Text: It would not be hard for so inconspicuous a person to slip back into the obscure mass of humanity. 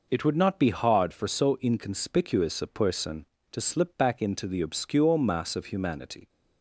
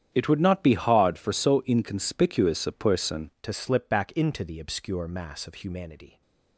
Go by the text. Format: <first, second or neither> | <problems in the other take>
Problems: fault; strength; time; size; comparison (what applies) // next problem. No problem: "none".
first | starts louder than the rest; strong; until 1.1 s; 10 dB // changes voice at "to"; from 3.4 s on; 2.8 s long